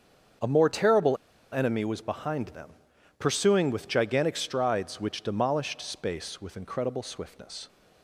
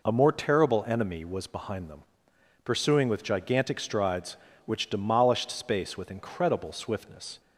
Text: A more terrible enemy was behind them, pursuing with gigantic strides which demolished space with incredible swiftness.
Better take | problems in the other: second | starts louder than the rest; strong; until 1.7 s; 7.5 dB // pauses between "terrible" and "enemy"; slight; at 1.1 s; 0.35 s long

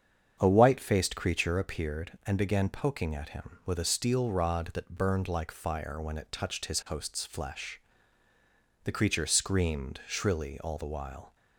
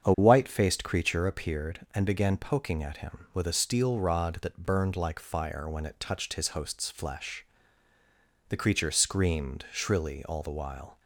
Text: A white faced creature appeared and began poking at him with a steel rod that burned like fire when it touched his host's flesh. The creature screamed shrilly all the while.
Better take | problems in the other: neither | starts louder than the rest; strong; the same in both

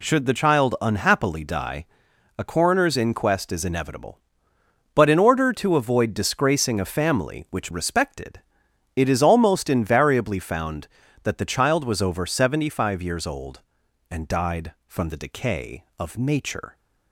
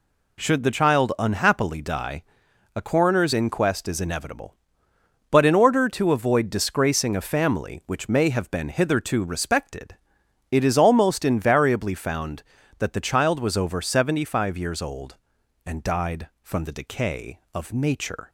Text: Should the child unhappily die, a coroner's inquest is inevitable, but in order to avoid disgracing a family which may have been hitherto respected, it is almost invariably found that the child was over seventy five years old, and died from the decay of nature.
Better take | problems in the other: second | skips "may have been hitherto"; at 7.7 s

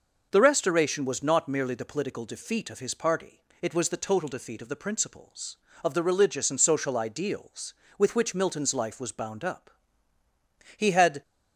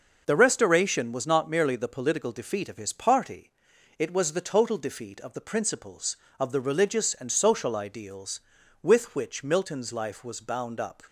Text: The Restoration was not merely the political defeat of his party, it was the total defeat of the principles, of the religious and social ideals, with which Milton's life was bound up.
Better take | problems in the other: second | goes on to say "He had"; slight; from 10.7 s on; 0.46 s long

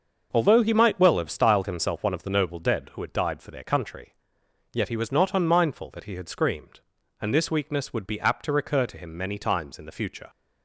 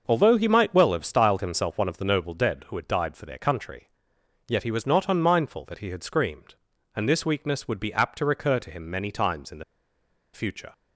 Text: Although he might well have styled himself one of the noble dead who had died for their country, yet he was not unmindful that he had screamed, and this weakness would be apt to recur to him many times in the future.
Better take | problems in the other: first | starts louder than the rest; until 1.0 s; 6 dB; also in the first // pauses between "the" and "future"; noticeable; at 9.6 s; 0.70 s long

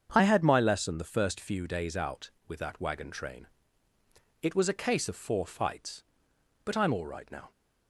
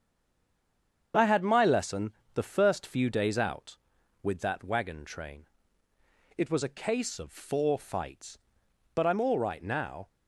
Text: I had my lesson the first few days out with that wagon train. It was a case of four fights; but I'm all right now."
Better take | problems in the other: first | stays silent before the first word; until 1.1 s; 1.1 s long // starts louder than the rest; strong; until 2.3 s; 7.5 dB; strong in the first // pauses between "lesson" and "the"; slight; at 2.1 s; 0.22 s long

